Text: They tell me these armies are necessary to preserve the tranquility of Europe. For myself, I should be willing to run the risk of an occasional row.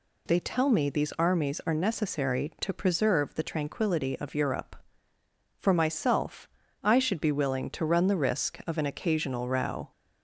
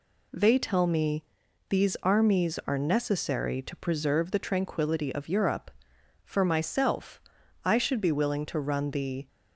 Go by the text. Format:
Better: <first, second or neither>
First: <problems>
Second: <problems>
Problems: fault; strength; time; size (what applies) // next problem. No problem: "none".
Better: first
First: none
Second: pauses between "me" and "these"; noticeable; at 1.2 s; 0.46 s long // stops before "risk of an occasional row"; at 9.2 s